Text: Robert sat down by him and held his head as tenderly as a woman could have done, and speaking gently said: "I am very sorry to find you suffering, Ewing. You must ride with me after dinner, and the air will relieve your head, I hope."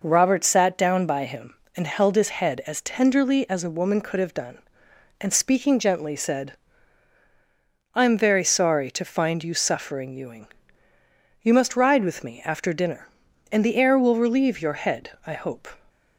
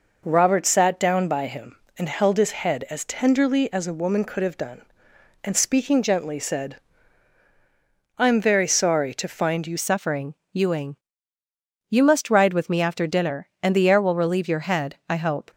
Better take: first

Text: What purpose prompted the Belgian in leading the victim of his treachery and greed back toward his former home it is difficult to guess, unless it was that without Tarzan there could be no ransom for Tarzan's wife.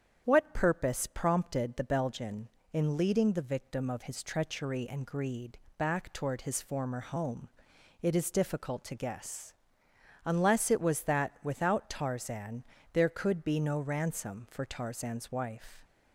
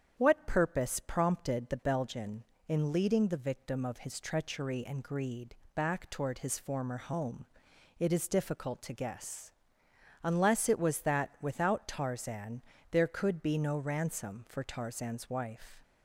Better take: neither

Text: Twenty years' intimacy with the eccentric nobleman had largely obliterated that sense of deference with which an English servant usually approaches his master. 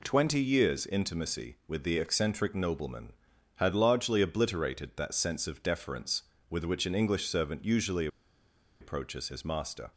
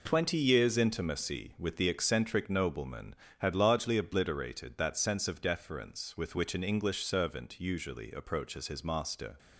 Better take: second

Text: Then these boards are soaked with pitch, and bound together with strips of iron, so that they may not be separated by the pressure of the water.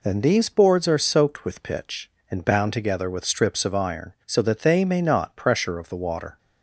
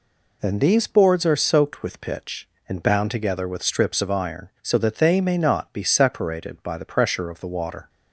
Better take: second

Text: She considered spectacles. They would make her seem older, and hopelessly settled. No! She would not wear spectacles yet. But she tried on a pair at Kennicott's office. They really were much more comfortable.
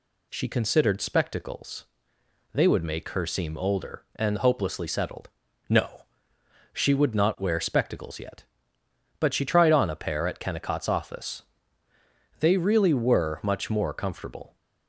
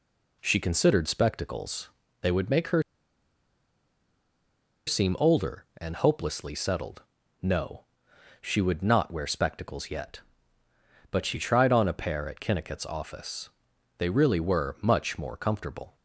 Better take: first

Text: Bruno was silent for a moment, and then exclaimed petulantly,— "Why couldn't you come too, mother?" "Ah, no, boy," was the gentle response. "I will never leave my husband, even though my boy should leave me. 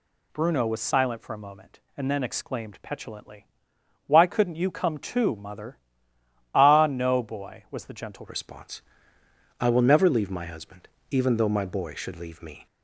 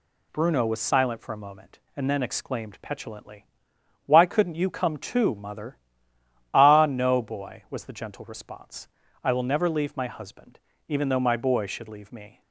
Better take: second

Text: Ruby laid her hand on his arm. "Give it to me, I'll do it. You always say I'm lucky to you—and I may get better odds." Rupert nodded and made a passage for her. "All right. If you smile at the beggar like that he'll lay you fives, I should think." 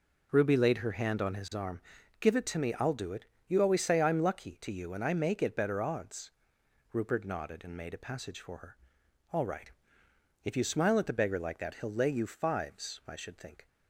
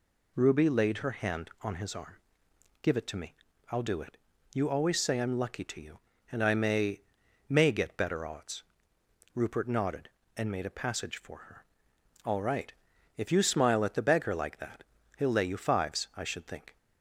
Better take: first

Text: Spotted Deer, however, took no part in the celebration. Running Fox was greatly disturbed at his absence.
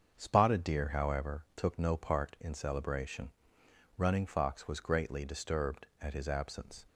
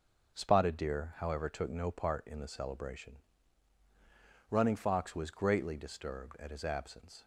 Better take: second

